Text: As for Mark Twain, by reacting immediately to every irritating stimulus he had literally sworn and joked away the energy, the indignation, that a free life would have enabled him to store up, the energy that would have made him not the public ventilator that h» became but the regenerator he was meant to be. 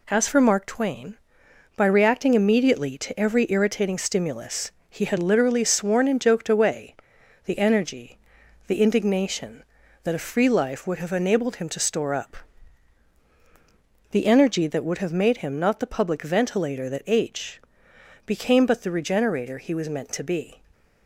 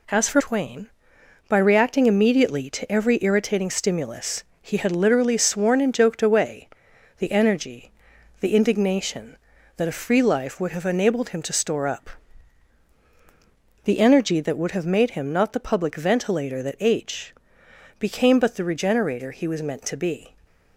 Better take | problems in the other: first | skips "Mark"; at 0.4 s // pauses between "stimulus" and "he"; slight; at 4.4 s; 0.20 s long; slight in the first // pauses between "away" and "the"; noticeable; at 6.6 s; 0.50 s long; noticeable in the first // pauses between "h" and "became"; noticeable; at 17.3 s; 0.64 s long; noticeable in the first

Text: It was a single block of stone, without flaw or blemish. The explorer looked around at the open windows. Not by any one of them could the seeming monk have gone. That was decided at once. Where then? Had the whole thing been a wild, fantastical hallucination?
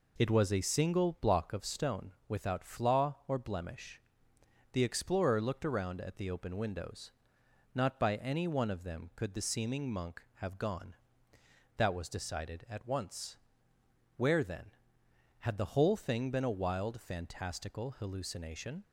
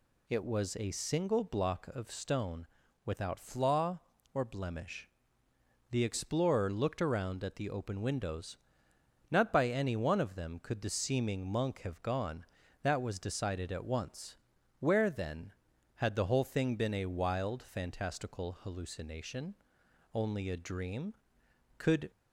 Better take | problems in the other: first | goes on to say "Only a dream Could"; strong; from 20.1 s on; 1.9 s long

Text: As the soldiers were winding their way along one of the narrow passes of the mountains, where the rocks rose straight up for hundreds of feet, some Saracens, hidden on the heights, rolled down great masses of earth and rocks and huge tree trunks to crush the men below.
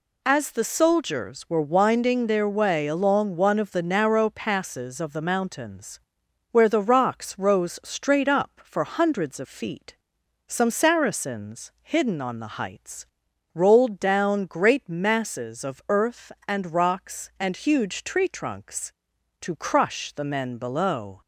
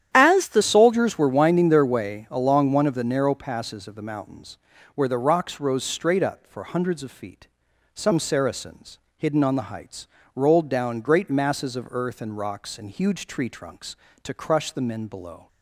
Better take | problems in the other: first | starts louder than the rest; strong; until 1.1 s; 10.5 dB // changes voice at "soldiers"; from 0.6 s on; 14.8 s long

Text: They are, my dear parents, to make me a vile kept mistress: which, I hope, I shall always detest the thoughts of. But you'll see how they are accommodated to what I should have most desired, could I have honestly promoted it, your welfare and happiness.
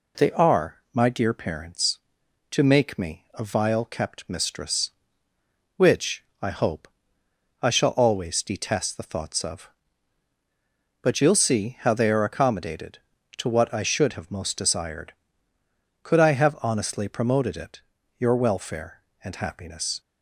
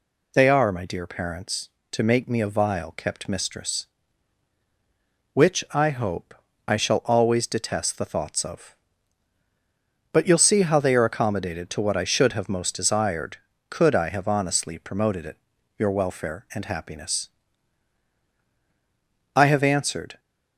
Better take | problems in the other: first | goes on to say "I have answered"; noticeable; from 19.3 s on; 0.84 s long

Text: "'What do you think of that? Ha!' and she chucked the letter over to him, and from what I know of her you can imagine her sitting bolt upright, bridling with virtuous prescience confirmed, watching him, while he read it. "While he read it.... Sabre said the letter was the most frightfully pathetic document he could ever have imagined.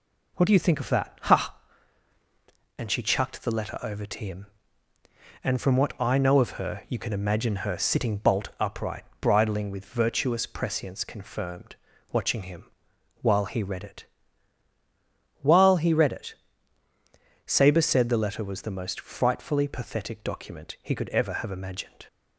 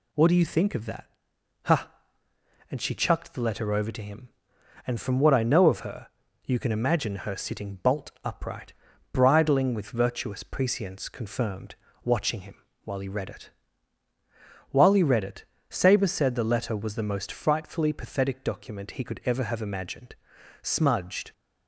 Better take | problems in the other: first | pauses between "her" and "you"; slight; at 6.0 s; 0.36 s long // goes on to say "Smudged"; noticeable; from 20.6 s on; 0.70 s long

